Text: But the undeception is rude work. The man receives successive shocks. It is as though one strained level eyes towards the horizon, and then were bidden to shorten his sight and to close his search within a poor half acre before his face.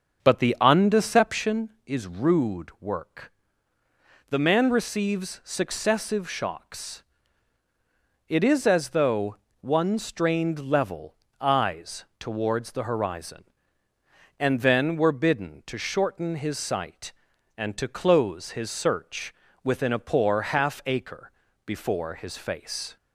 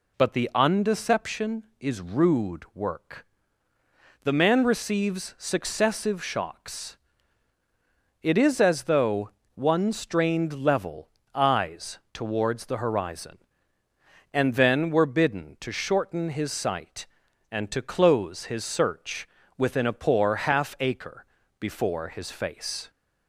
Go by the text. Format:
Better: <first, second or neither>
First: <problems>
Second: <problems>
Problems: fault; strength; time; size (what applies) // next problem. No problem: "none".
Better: second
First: starts louder than the rest; until 1.8 s; 6.5 dB // pauses between "though" and "one"; slight; at 9.3 s; 0.24 s long // pauses between "level" and "eyes"; slight; at 11.1 s; 0.26 s long // pauses between "search" and "within"; slight; at 19.3 s; 0.30 s long // pauses between "acre" and "before"; slight; at 21.3 s; 0.34 s long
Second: pauses between "though" and "one"; slight; at 9.2 s; 0.24 s long // pauses between "level" and "eyes"; slight; at 11.0 s; 0.26 s long // pauses between "search" and "within"; slight; at 19.2 s; 0.30 s long // pauses between "acre" and "before"; slight; at 21.2 s; 0.34 s long